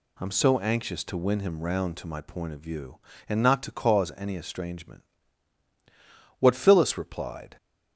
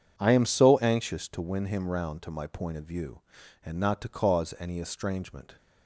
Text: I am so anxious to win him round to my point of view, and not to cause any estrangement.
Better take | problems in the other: second | goes on to say "What Phyllis replied"; noticeable; from 6.3 s on; 1.1 s long

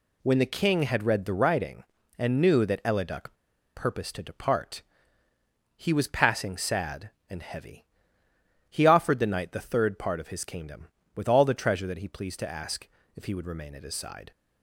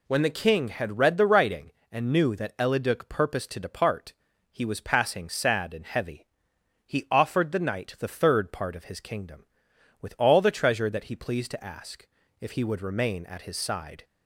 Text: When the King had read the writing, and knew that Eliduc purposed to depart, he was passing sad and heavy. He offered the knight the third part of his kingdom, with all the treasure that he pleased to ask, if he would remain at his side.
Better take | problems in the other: second | pauses between "Eliduc" and "purposed"; at 3.3 s; 0.43 s long

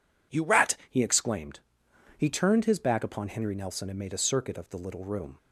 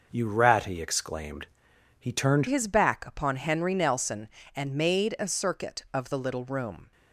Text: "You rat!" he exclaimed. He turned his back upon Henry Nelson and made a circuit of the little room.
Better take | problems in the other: first | changes voice at "his"; from 2.4 s on; 4.5 s long

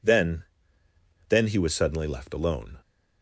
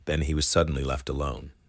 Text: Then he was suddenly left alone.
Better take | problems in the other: second | says "Then" twice; at 1.2 s

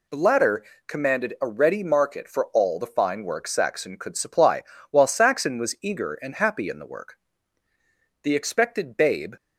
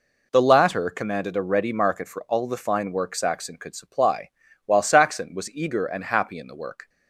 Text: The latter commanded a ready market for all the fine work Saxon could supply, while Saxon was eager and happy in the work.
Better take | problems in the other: second | pauses between "latter" and "commanded"; slight; at 0.6 s; 0.22 s long // goes on to say "The expected babe"; noticeable; from 8.2 s on; 1.1 s long

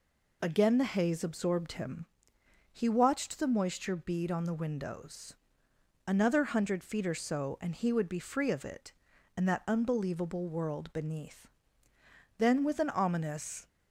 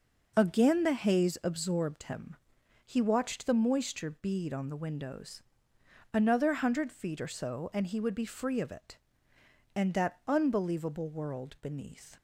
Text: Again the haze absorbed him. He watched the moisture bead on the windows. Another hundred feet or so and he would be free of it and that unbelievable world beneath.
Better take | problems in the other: second | goes on to say "Then with an ominous"; noticeable; from 12.3 s on; 1.3 s long

